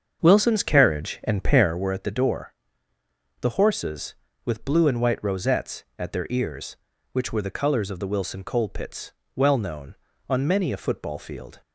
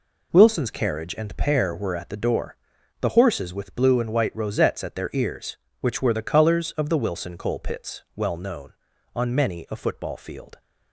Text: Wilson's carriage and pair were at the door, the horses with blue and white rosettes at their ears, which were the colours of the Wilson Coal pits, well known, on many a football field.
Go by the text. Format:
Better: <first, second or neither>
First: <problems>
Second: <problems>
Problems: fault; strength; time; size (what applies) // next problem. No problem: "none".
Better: second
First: starts louder than the rest; until 1.9 s; 7 dB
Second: none